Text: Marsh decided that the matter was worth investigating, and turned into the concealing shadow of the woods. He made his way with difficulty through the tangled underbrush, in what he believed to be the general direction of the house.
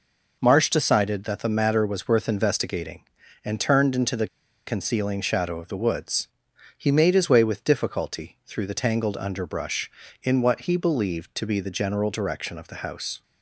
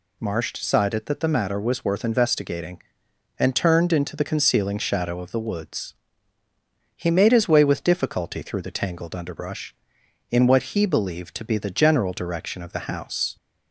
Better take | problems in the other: second | pauses between "the" and "concealing"; at 4.2 s; 0.40 s long

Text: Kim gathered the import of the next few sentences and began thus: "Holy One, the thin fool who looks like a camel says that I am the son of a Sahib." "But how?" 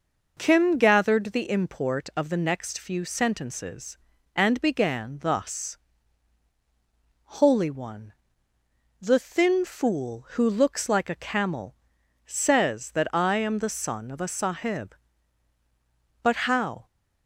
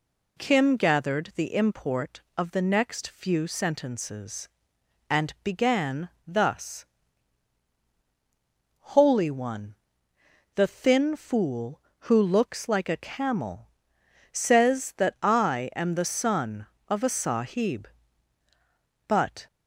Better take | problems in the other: first | pauses between "began" and "thus"; slight; at 6.1 s; 0.16 s long // pauses between "camel" and "says"; noticeable; at 13.7 s; 0.60 s long; noticeable in the first // stops before "how"; at 19.4 s

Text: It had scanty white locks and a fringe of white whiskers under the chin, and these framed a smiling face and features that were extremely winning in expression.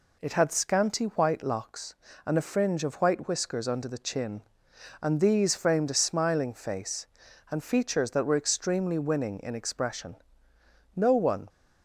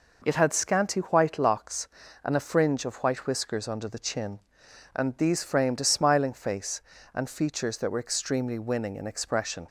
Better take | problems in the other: second | goes on to say "No one"; from 10.9 s on; 0.54 s long

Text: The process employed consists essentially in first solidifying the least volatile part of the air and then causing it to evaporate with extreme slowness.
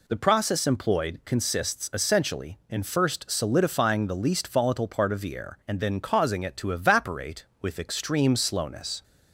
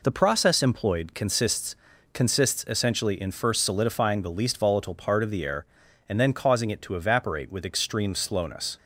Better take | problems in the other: first | says "consists" twice; at 2.1 s

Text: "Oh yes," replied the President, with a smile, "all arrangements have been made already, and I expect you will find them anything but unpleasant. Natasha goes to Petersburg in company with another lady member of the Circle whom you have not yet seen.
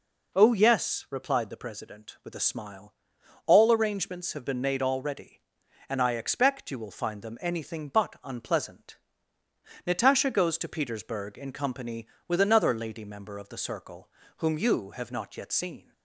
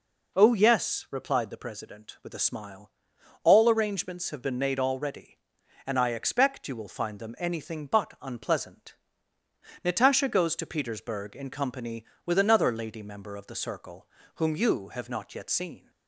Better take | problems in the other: neither | pauses between "Circle" and "whom"; slight; the same in both

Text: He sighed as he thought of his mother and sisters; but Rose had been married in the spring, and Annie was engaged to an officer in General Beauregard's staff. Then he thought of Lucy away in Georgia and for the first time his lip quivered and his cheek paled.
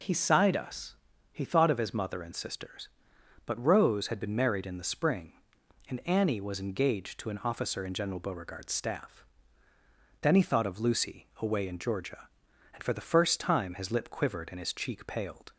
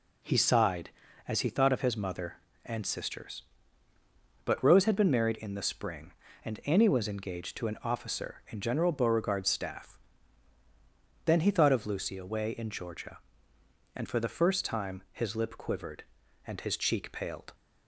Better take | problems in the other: second | says "us" for "as"; at 0.5 s

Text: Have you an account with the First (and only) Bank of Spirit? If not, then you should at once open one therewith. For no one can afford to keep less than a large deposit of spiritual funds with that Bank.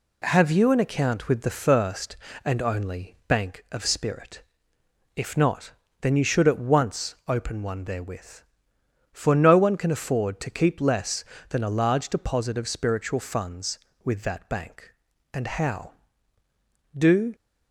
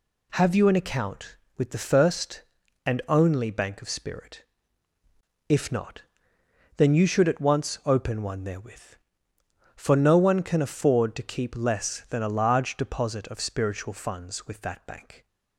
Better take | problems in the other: second | goes on to say "And how do"; strong; from 15.3 s on; 2.0 s long

